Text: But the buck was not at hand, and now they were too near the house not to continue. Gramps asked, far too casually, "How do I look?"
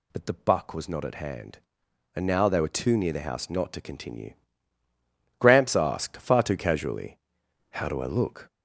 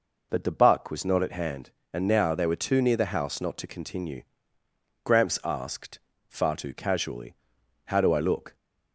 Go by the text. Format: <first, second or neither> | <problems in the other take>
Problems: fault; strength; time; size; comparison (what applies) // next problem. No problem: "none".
second | gets louder; noticeable; throughout; 4.5 dB